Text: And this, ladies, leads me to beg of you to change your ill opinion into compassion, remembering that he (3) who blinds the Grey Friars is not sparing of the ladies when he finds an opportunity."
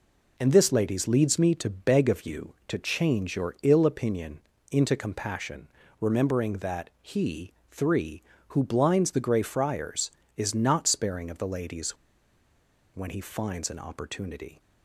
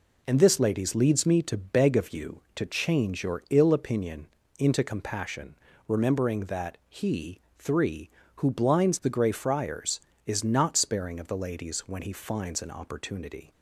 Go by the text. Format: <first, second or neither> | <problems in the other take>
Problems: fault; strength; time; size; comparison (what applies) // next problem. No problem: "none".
second | pauses between "opinion" and "into"; slight; at 4.3 s; 0.32 s long; slight in the second // pauses between "ladies" and "when"; at 11.9 s; 0.98 s long